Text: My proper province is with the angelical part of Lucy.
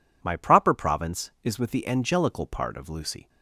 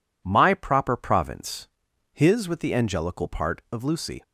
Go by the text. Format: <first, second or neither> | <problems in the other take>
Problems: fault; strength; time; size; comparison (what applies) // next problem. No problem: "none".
first | says "his" for "is"; at 2.1 s